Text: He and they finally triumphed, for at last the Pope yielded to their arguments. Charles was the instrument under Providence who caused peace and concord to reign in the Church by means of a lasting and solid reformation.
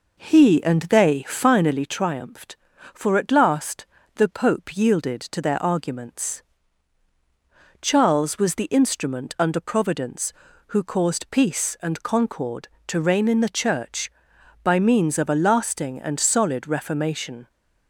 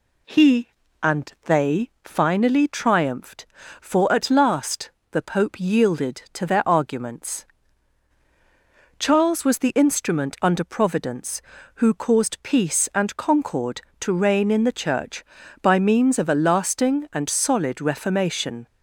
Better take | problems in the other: second | starts louder than the rest; noticeable; until 1.9 s; 5 dB // pauses between "last" and "the"; slight; at 3.8 s; 0.30 s long; slight in the second

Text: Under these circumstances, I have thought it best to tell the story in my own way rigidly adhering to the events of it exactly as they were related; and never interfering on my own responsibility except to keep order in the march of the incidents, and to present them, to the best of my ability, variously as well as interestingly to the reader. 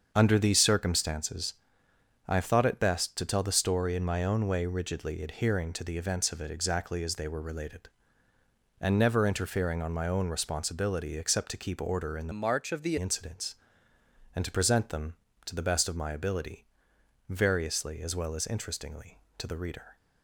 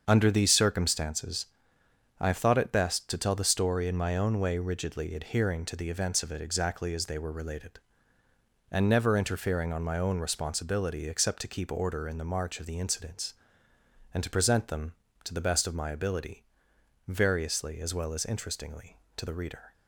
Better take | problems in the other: second | starts louder than the rest; until 1.1 s; 7 dB; also in the second // changes voice from "march" to "the"; from 12.3 to 12.9 s; 0.6 s long

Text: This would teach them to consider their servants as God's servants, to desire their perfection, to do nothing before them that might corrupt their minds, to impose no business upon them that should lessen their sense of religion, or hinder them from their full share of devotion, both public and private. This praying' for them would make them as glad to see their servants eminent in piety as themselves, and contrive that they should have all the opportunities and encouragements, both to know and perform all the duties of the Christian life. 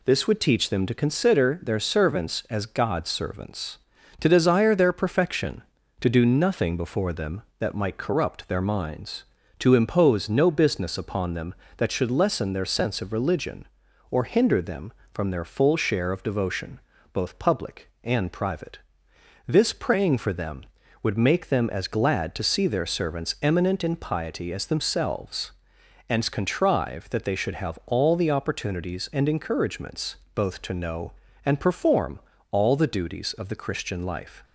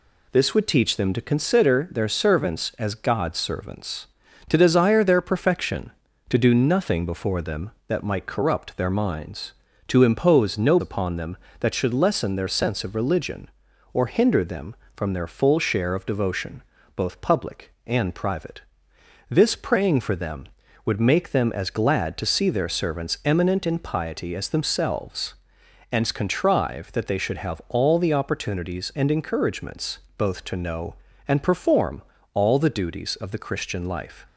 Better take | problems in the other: first | skips "business"; at 10.7 s // pauses between "perform" and "all"; slight; at 32.0 s; 0.32 s long; slight in the first

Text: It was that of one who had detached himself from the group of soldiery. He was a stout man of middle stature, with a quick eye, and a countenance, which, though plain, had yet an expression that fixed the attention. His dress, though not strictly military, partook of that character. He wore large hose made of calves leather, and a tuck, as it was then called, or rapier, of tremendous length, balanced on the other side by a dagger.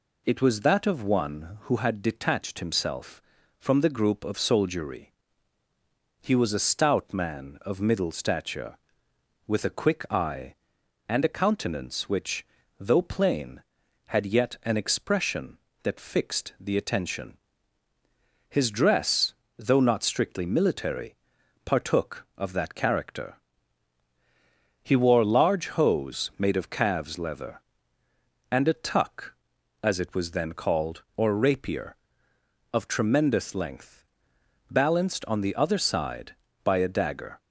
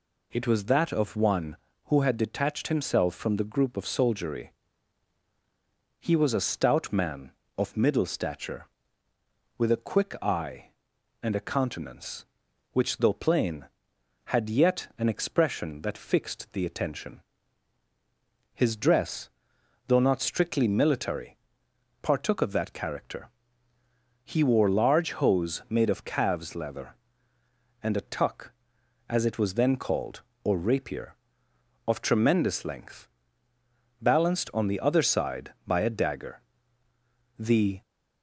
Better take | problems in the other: first | goes on to say "The"; slight; from 37.3 s on; 0.44 s long

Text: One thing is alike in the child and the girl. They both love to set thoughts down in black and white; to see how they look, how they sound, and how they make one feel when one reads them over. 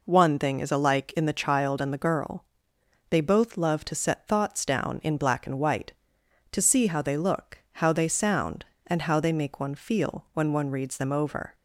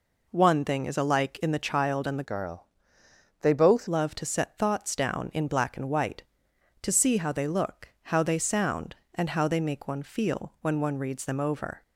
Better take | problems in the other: first | changes voice from "girl" to "both"; from 2.2 to 3.8 s; 1.6 s long

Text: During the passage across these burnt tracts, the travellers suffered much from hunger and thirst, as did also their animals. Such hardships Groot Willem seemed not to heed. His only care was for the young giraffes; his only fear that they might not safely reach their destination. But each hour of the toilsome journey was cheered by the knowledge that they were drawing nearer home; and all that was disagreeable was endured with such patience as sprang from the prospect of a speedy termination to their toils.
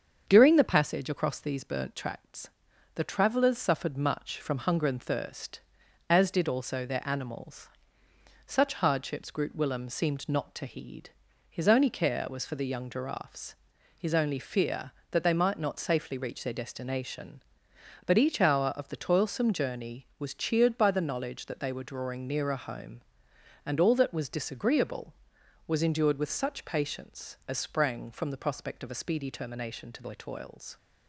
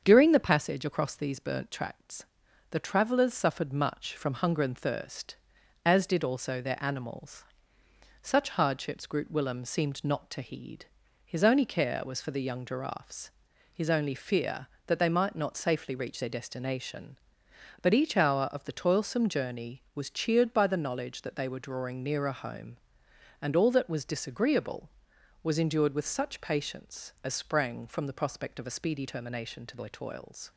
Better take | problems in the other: neither | starts louder than the rest; strong; the same in both

